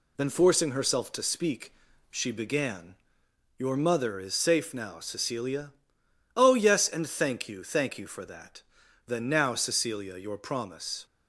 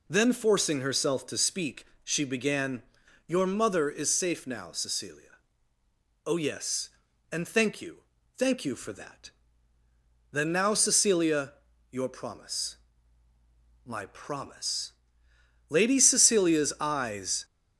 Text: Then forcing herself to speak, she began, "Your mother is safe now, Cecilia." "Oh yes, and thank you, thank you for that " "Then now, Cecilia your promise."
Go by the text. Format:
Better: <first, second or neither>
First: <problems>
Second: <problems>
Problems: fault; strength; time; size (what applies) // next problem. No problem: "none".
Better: first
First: none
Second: pauses between "Cecilia" and "your"; at 11.5 s; 0.38 s long // goes on to say "My promise Lady Cecilia's eyes"; strong; from 13.8 s on; 3.6 s long